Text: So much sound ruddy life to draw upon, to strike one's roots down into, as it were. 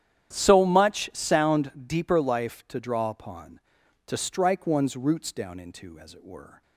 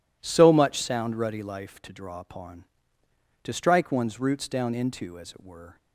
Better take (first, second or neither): second